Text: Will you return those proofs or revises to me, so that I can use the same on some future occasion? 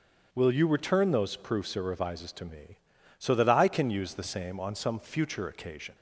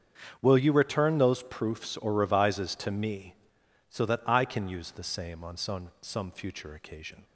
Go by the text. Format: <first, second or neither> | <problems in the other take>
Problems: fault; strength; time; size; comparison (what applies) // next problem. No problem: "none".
first | starts louder than the rest; strong; until 1.4 s; 7.5 dB; strong in the first // says "some" twice; at 6.0 s